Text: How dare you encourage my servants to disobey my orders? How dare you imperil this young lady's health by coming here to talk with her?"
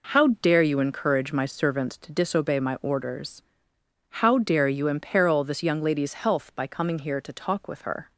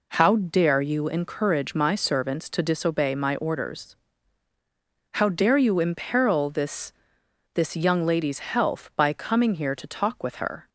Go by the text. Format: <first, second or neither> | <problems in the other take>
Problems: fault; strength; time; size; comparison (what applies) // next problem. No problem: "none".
first | says "this" twice; at 7.5 s